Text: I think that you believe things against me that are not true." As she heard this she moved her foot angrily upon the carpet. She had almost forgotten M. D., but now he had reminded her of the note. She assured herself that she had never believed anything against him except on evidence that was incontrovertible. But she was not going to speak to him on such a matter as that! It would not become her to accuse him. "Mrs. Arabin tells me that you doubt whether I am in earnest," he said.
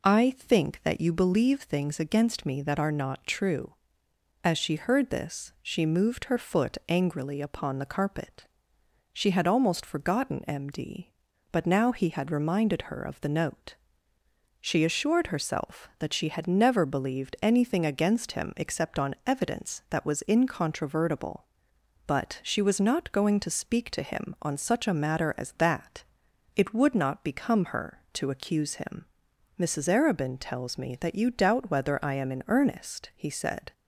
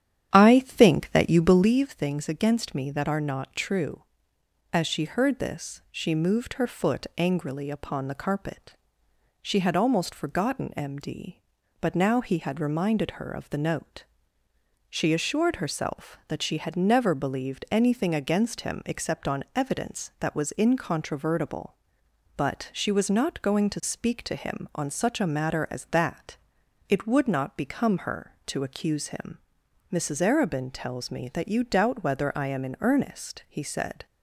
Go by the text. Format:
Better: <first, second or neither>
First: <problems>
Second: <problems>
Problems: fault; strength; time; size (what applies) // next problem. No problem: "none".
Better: first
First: none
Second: starts louder than the rest; strong; until 1.7 s; 10 dB